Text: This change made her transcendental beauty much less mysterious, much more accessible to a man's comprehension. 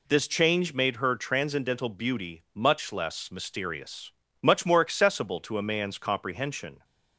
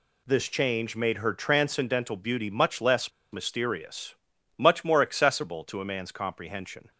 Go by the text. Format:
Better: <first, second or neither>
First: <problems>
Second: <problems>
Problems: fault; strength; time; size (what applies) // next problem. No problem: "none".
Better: first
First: none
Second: pauses between "less" and "mysterious"; slight; at 3.1 s; 0.21 s long